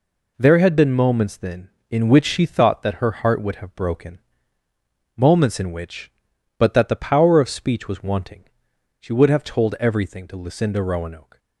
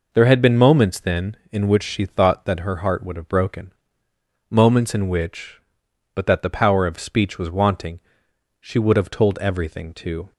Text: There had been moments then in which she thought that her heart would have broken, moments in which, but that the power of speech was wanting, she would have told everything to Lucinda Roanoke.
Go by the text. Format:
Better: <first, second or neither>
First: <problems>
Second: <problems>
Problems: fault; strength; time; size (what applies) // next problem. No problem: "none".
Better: first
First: none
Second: stops before "Lucinda Roanoke"; at 10.3 s